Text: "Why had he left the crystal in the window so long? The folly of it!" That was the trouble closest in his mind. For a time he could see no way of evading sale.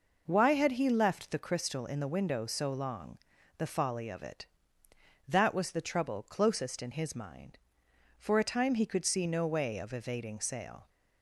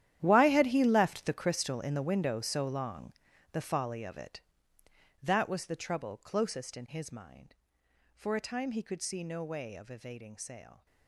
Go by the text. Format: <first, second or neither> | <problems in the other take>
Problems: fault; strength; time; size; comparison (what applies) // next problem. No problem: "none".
first | gets quieter; strong; throughout; 16.5 dB